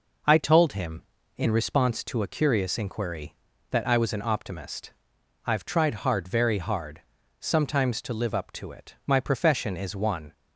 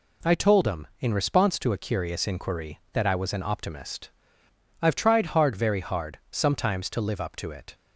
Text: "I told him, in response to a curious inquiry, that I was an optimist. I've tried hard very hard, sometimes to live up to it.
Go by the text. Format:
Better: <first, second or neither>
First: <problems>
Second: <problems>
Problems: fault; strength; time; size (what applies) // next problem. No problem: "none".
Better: second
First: goes on to say "My profession is one"; noticeable; from 9.0 s on; 1.2 s long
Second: none